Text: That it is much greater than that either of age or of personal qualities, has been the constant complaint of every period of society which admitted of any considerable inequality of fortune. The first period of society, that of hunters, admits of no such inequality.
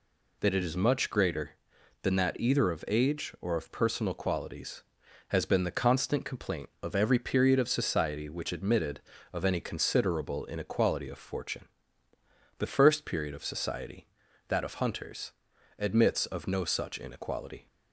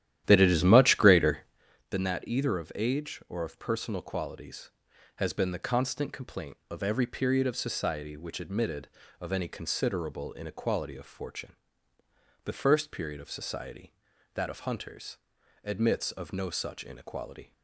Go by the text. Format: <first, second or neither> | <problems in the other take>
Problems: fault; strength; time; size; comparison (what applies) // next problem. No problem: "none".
first | starts louder than the rest; strong; until 1.6 s; 12 dB